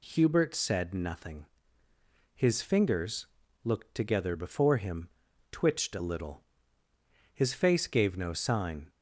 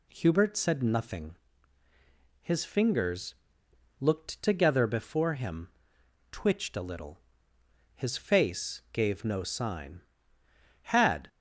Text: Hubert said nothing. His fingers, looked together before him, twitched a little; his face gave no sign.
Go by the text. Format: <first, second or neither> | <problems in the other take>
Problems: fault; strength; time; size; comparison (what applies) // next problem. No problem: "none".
first | goes on to say "Had"; slight; from 10.7 s on; 0.48 s long